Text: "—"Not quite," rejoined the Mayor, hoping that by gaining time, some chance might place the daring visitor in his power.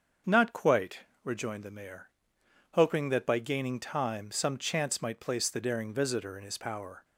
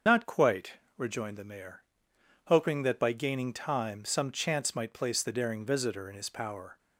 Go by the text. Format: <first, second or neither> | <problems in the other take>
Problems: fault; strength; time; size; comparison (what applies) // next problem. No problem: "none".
first | loses the start of "Not"; at 0.0 s; 65 ms // starts louder than the rest; until 1.3 s; 6.5 dB; also in the first